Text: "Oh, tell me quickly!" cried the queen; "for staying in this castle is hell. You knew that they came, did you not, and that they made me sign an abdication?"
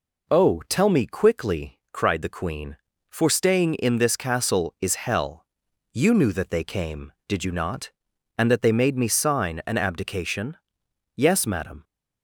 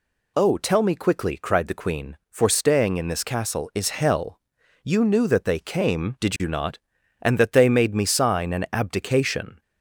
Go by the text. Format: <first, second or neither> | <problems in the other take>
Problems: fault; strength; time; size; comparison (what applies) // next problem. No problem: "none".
second | goes on to say "Yes madam"; noticeable; from 11.1 s on; 0.68 s long